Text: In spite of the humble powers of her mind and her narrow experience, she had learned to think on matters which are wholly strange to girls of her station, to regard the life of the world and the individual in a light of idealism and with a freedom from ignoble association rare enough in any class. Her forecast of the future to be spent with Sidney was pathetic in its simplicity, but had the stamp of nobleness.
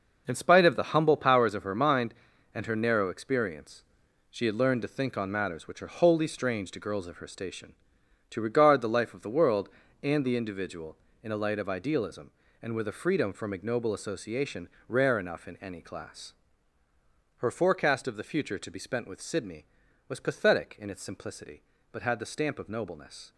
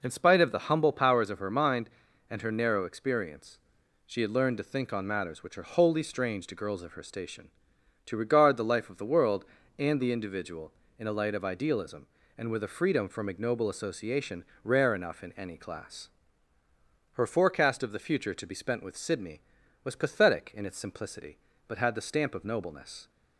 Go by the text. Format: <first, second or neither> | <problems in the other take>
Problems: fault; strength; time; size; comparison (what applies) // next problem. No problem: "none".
second | gets quieter; strong; throughout; 9.5 dB // pauses between "association" and "rare"; slight; at 14.6 s; 0.22 s long; slight in the second